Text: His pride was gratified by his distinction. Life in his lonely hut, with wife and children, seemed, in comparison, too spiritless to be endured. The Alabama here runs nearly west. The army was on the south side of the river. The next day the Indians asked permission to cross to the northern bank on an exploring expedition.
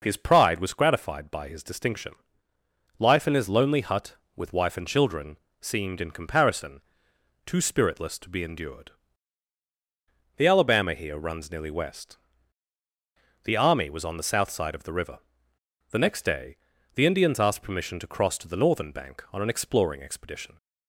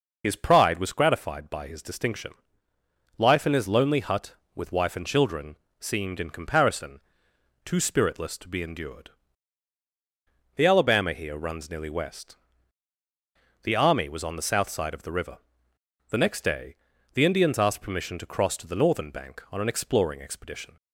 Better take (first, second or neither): first